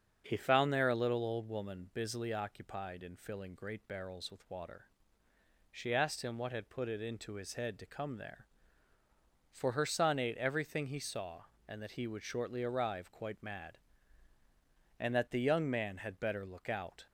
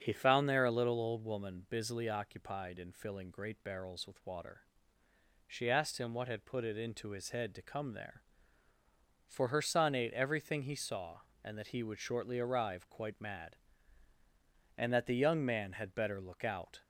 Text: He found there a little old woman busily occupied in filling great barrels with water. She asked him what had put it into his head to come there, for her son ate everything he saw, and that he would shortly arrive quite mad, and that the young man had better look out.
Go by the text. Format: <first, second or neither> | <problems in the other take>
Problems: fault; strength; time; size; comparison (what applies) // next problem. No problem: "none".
neither | starts louder than the rest; strong; the same in both